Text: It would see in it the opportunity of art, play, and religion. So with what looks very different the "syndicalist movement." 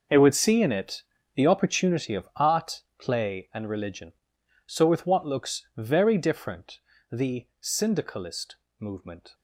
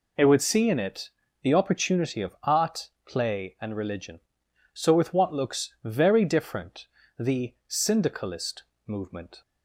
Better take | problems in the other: second | gets quieter; strong; throughout; 15 dB // pauses between "it" and "the"; slight; at 1.0 s; 0.32 s long; slight in the second // pauses between "different" and "the"; slight; at 6.7 s; 0.32 s long; slight in the second // pauses between "syndicalist" and "movement"; slight; at 8.5 s; 0.22 s long; slight in the second

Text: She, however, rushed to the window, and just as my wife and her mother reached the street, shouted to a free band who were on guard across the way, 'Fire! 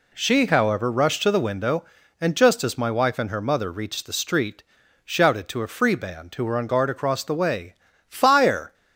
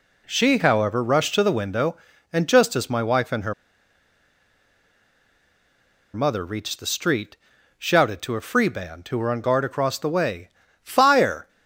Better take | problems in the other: first | pauses between "her" and "mother"; strong; at 3.5 s; 2.6 s long

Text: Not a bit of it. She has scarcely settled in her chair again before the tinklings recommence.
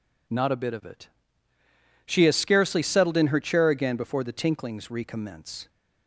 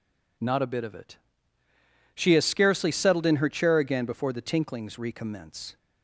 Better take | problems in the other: neither | none

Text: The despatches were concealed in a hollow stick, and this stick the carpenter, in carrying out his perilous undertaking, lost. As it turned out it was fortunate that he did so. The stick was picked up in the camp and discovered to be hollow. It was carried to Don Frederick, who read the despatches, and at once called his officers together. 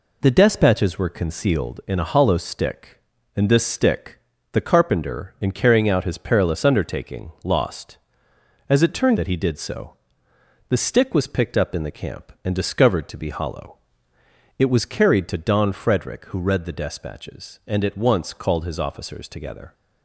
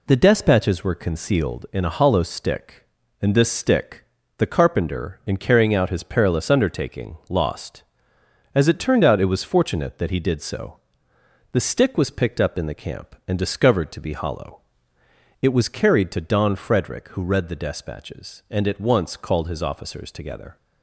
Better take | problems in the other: second | pauses between "stick" and "the"; slight; at 4.1 s; 0.34 s long; slight in the second // skips "out it was fortunate"; at 9.1 s

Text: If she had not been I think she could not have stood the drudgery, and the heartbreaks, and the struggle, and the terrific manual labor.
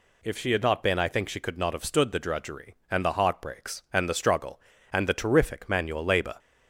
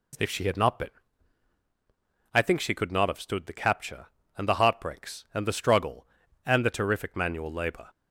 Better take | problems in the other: first | pauses between "been" and "I"; strong; at 0.8 s; 1.4 s long // says "capture" for "drudgery"; at 3.5 s

